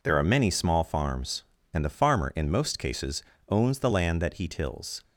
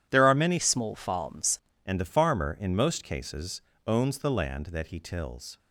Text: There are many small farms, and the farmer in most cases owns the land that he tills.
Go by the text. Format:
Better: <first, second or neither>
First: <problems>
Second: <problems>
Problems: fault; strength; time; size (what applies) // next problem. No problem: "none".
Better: first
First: pauses between "cases" and "owns"; slight; at 3.2 s; 0.28 s long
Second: changes voice from "small" to "farms"; from 0.5 to 1.5 s; 1.0 s long // pauses between "cases" and "owns"; slight; at 3.6 s; 0.24 s long